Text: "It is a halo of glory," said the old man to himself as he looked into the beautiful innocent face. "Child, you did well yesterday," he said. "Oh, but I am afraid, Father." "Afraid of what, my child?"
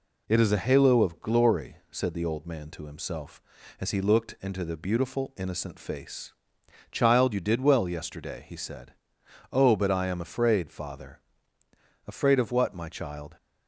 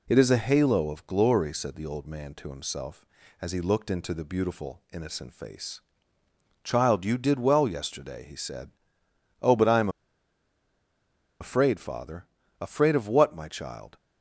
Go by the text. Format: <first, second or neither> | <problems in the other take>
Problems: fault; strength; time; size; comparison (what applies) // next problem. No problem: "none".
first | pauses between "am" and "afraid"; strong; at 9.8 s; 1.5 s long